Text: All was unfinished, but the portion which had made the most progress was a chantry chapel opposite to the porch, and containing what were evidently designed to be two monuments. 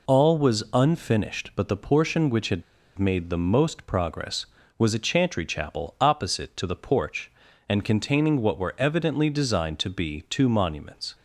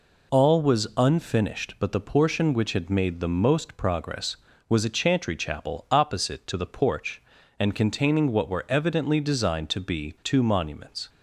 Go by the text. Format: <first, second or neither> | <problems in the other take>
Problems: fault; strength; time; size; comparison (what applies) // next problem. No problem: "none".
second | pauses between "had" and "made"; slight; at 2.6 s; 0.34 s long